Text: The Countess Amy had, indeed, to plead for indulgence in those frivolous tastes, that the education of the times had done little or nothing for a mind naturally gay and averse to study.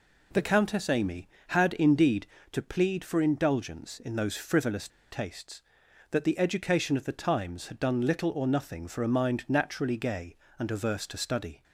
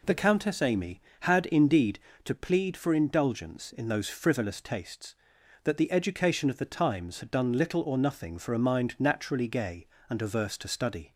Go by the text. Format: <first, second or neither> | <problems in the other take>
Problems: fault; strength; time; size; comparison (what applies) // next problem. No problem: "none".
second | pauses between "frivolous" and "tastes"; slight; at 4.8 s; 0.22 s long